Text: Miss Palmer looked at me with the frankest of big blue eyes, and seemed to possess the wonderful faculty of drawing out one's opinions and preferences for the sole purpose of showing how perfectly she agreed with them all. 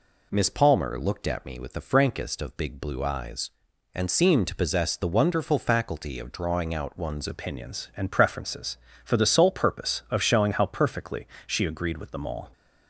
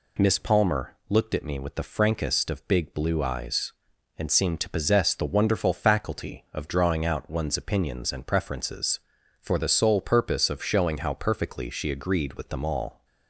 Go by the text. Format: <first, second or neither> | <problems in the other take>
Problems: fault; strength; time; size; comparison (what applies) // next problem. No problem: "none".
second | changes voice at "opinions"; from 7.2 s on; 5.3 s long // pauses between "perfectly" and "she"; slight; at 11.2 s; 0.20 s long